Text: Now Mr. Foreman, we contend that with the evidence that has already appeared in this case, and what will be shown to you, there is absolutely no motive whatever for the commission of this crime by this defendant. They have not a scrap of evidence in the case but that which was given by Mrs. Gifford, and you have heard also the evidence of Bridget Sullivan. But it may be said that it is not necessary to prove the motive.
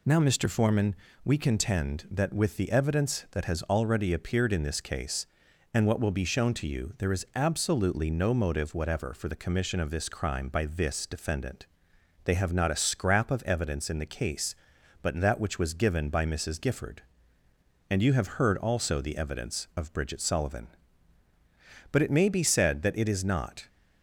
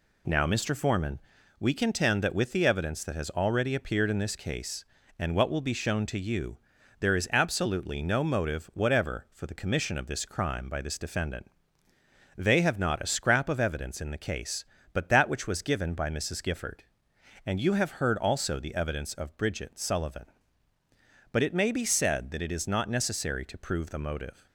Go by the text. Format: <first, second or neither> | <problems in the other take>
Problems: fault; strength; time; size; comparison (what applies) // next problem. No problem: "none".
second | stops before "necessary to prove the motive"; at 23.6 s